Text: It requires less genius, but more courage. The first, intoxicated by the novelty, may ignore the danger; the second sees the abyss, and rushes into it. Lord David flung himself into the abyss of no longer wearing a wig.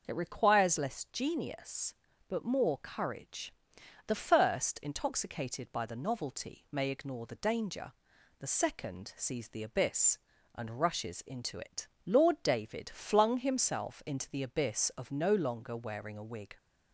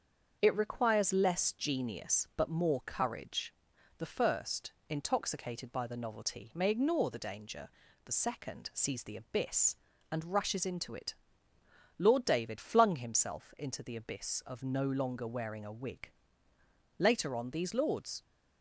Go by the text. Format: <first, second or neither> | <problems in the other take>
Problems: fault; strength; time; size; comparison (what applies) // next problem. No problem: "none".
first | starts louder than the rest; until 1.4 s; 7 dB; noticeable in the first // goes on to say "Later on these lords"; noticeable; from 16.9 s on; 1.2 s long